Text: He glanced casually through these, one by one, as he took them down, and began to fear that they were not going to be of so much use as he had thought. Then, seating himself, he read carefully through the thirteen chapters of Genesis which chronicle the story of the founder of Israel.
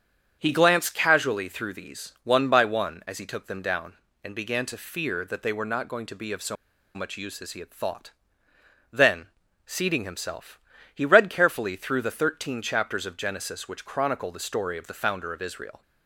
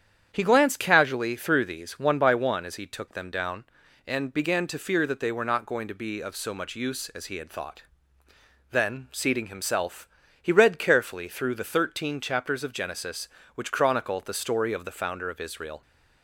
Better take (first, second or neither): second